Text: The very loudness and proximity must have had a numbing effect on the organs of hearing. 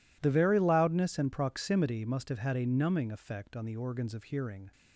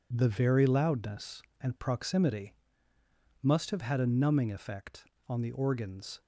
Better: first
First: none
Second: pauses between "proximity" and "must"; noticeable; at 2.5 s; 0.88 s long // stops before "of hearing"; at 6.2 s

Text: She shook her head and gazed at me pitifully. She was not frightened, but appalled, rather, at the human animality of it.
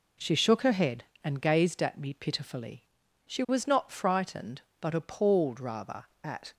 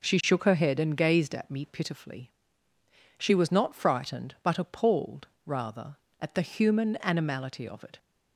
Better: second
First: stops before "the human animality of it"; at 6.5 s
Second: none

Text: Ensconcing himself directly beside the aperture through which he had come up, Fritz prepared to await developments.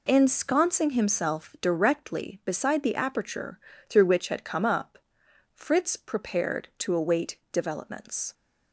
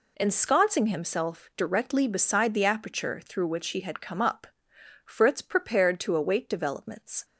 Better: second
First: pauses between "aperture" and "through"; slight; at 3.5 s; 0.30 s long // skips "he"; at 4.2 s // pauses between "await" and "developments"; slight; at 7.3 s; 0.16 s long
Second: none

